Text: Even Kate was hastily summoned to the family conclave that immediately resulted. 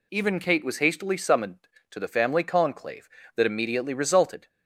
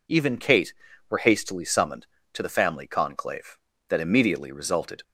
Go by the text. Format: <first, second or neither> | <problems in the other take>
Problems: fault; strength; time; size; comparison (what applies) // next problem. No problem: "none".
first | says "were" for "was"; at 1.0 s